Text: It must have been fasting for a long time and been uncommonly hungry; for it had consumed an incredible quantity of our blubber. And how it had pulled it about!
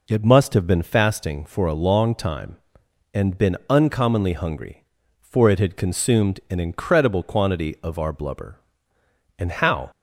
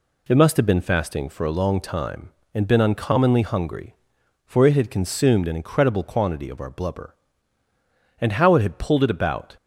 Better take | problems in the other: second | stops before "it had pulled it about"; at 9.9 s

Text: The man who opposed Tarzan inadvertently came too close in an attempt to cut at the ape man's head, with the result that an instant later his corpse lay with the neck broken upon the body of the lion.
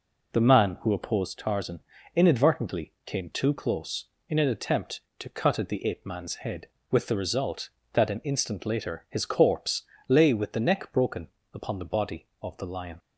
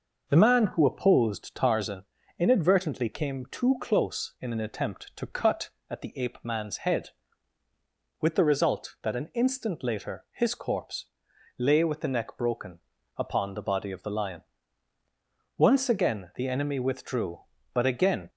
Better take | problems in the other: first | pauses between "Tarzan" and "inadvertently"; slight; at 2.0 s; 0.34 s long; slight in the first // pauses between "corpse" and "lay"; noticeable; at 11.0 s; 0.52 s long; slight in the first // pauses between "broken" and "upon"; slight; at 12.7 s; 0.36 s long; slight in the first // goes on to say "Once again the enemy withdrew but again"; strong; from 15.5 s on; 2.7 s long

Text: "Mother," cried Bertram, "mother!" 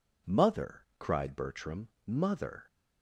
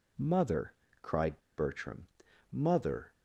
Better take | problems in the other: first | pauses between "cried" and "Bertram"; slight; at 1.4 s; 0.16 s long

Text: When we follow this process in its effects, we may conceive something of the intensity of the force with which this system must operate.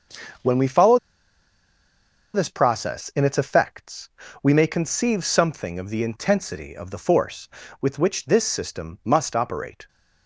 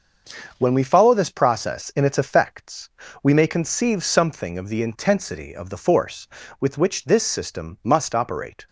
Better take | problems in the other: second | starts louder than the rest; until 2.7 s; 6.5 dB; also in the second // pauses between "follow" and "this"; strong; at 0.9 s; 1.3 s long

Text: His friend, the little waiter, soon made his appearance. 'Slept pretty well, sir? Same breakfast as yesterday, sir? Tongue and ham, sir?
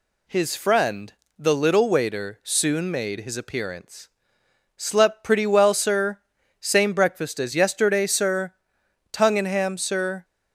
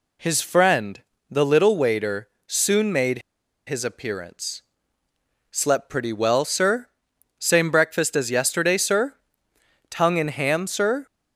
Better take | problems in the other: first | pauses between "made" and "his"; noticeable; at 3.2 s; 0.48 s long

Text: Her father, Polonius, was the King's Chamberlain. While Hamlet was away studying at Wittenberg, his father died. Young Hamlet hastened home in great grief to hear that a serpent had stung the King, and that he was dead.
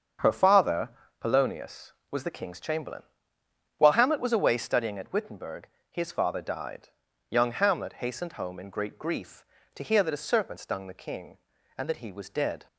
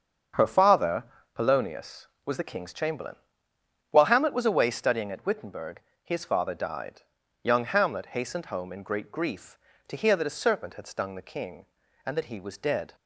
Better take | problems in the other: second | starts louder than the rest; until 1.4 s; 7 dB; also in the second // skips "had"; at 10.5 s

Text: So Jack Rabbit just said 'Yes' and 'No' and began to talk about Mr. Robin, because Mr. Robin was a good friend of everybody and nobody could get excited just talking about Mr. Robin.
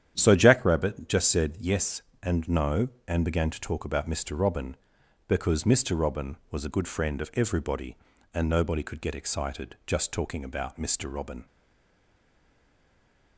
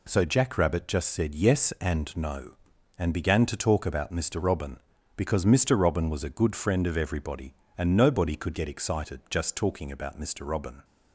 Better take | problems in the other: second | starts louder than the rest; strong; until 1.1 s; 9.5 dB // stays silent after the last word; noticeable; from 11.4 s on; 1.9 s long

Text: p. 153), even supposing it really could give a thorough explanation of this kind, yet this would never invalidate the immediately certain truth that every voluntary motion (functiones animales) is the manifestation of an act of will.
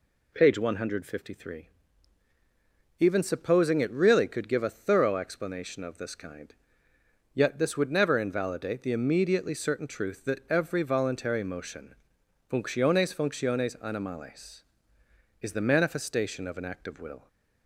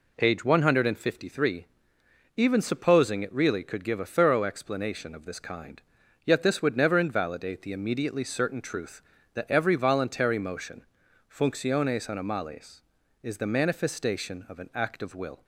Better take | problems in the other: second | says "functiones" twice; at 13.1 s

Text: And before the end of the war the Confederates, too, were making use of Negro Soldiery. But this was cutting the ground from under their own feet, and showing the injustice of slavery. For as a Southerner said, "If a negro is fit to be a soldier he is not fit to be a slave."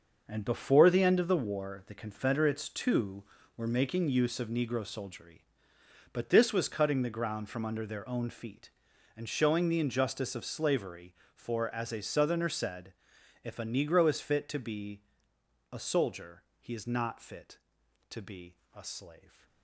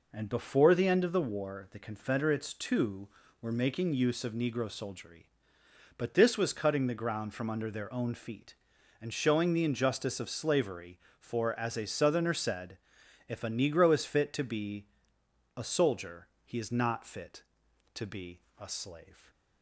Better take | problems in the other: second | gets quieter; strong; throughout; 10.5 dB // pauses between "be" and "a"; noticeable; at 15.0 s; 0.70 s long; noticeable in the second // pauses between "soldier" and "he"; slight; at 16.4 s; 0.16 s long; slight in the second // pauses between "be" and "a"; slight; at 18.5 s; 0.18 s long; slight in the second

